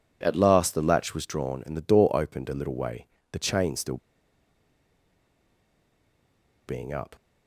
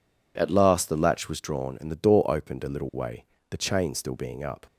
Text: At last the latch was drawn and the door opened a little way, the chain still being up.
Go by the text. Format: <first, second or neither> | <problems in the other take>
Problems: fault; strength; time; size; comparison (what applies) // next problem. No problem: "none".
second | pauses between "still" and "being"; strong; at 3.9 s; 2.6 s long